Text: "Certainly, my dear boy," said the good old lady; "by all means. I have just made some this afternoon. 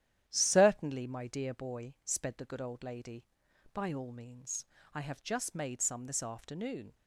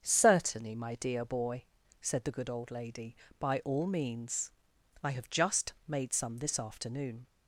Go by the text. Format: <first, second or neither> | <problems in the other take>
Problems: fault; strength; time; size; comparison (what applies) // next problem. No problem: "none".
second | starts louder than the rest; strong; until 1.2 s; 11 dB; also in the second // says "sped" for "said"; at 2.0 s